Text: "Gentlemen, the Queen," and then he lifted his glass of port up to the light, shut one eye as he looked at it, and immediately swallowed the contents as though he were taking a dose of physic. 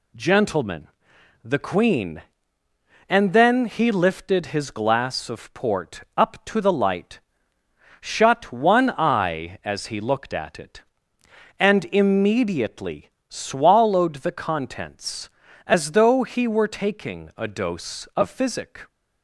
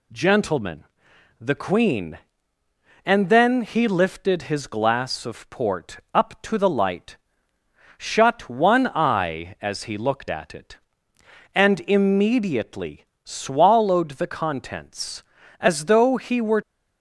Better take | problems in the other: first | pauses between "immediately" and "swallowed"; slight; at 13.0 s; 0.20 s long; slight in the first // stops before "taking a dose of physic"; at 16.6 s

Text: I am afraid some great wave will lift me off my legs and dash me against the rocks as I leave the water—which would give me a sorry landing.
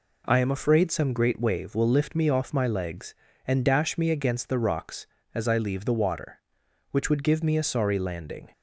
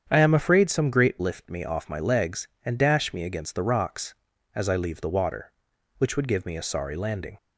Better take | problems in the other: first | starts louder than the rest; strong; until 1.1 s; 8 dB // skips "wave will"; at 1.1 s

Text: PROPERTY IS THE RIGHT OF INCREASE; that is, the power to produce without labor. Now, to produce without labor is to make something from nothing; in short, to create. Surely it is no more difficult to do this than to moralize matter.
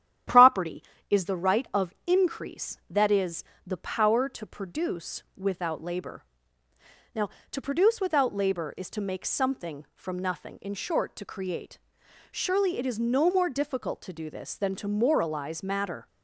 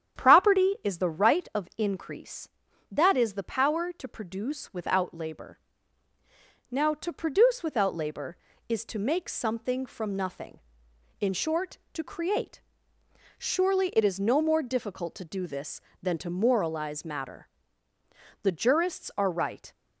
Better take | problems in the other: first | starts louder than the rest; strong; until 1.2 s; 9 dB; strong in the first // goes on to say "The jurists are right"; noticeable; from 18.4 s on; 1.3 s long

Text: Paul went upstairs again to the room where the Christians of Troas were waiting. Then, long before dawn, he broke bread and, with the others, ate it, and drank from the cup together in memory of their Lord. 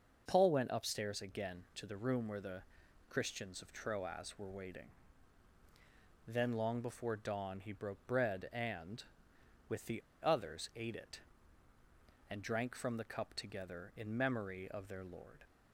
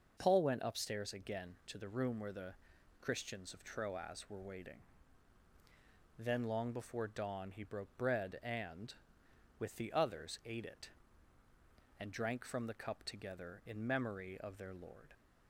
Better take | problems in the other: second | starts louder than the rest; noticeable; until 1.2 s; 6 dB; noticeable in the second // pauses between "the" and "Christians"; noticeable; at 2.6 s; 0.46 s long; noticeable in the second // pauses between "the" and "others"; slight; at 10.0 s; 0.22 s long

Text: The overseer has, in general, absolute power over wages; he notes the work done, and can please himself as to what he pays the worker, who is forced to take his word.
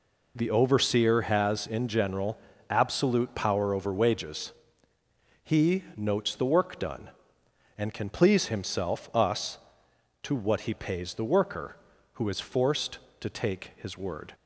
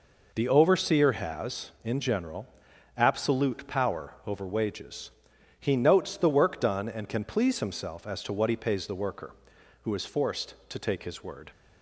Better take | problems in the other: second | says "us" for "as"; at 9.1 s

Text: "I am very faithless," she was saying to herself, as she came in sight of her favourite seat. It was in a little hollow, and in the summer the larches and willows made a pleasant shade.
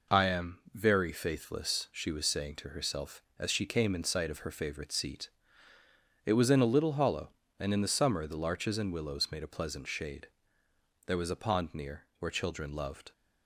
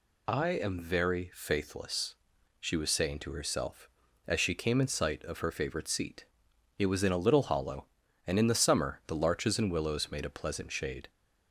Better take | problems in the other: second | goes on to say "There was a pond near where children loved"; strong; from 11.0 s on; 2.0 s long

